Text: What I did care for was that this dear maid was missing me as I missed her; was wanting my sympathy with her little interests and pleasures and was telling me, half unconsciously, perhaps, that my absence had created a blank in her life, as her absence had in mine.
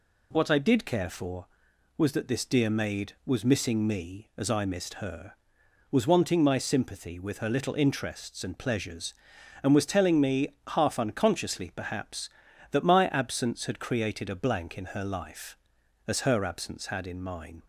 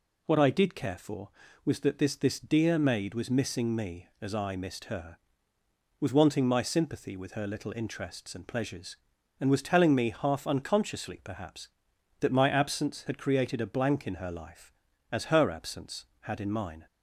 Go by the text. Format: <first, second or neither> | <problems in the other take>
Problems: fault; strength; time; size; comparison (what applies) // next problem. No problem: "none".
first | says "this" twice; at 2.1 s